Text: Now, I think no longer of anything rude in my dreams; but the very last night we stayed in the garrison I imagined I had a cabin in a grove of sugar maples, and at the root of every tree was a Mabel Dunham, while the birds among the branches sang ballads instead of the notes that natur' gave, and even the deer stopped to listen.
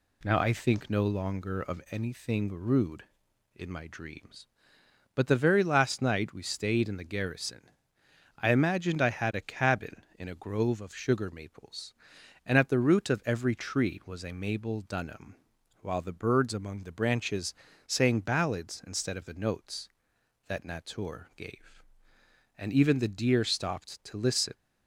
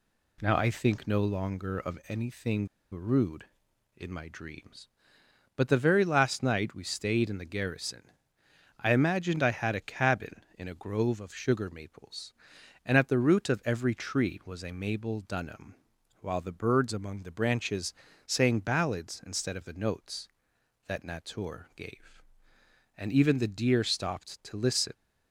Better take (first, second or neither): first